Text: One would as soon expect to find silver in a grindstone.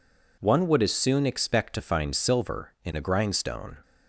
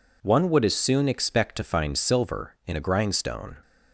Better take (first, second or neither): neither